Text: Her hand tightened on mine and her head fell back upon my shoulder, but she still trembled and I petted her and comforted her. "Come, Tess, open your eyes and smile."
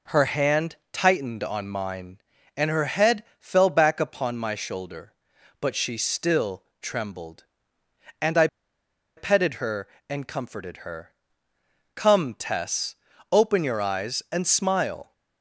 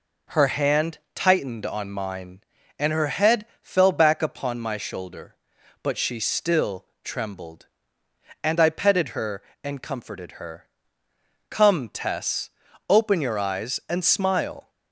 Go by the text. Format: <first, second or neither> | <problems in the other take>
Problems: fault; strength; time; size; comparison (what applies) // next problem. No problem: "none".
second | pauses between "hand" and "tightened"; slight; at 0.7 s; 0.16 s long; slight in the second // pauses between "head" and "fell"; slight; at 3.2 s; 0.16 s long; slight in the second // pauses between "still" and "trembled"; slight; at 6.6 s; 0.18 s long; slight in the second // pauses between "I" and "petted"; noticeable; at 8.4 s; 0.70 s long